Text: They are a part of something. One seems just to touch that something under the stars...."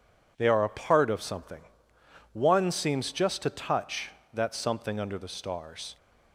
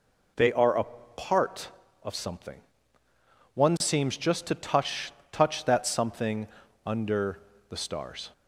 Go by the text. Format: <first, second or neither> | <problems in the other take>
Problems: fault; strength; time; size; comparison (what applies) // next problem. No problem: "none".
first | pauses between "a" and "part"; slight; at 0.8 s; 0.32 s long // says "touch" twice; at 5.3 s // pauses between "something" and "under"; at 6.4 s; 0.38 s long // pauses between "under" and "the"; slight; at 7.3 s; 0.30 s long